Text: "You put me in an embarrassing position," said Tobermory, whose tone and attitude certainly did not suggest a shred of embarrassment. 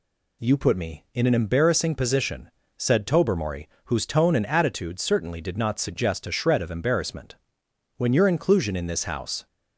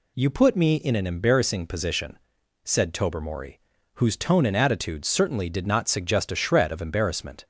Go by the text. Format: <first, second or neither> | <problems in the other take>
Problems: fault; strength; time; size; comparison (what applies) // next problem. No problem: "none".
second | goes on to say "When your inclusion in this house"; from 7.9 s on; 1.5 s long